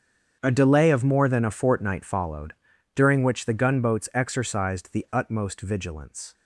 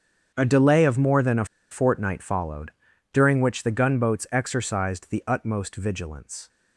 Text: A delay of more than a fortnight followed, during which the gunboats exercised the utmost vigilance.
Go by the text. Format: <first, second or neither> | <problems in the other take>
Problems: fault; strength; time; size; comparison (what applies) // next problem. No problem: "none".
first | starts louder than the rest; strong; until 1.3 s; 7.5 dB; strong in the first // pauses between "a" and "fortnight"; slight; at 1.4 s; 0.26 s long